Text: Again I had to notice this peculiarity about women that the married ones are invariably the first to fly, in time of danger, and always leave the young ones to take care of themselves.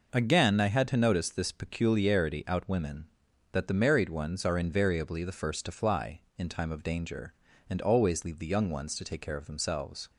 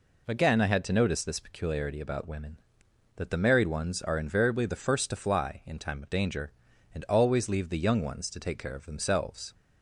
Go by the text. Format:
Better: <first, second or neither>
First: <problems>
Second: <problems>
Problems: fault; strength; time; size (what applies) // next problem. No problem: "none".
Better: second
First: says "out" for "about"; at 2.4 s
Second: none